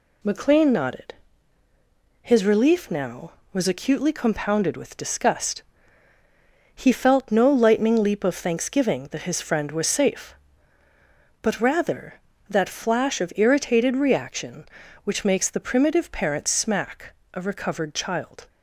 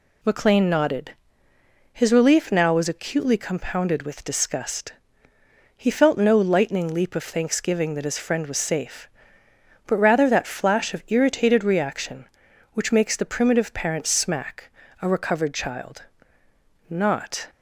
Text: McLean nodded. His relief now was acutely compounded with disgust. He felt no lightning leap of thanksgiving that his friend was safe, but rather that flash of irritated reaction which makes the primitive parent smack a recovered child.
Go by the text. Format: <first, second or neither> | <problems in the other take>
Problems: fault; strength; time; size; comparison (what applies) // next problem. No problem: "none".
first | pauses between "smack" and "a"; slight; at 14.6 s; 0.30 s long; slight in the first // goes on to say "Not"; from 16.8 s on; 0.60 s long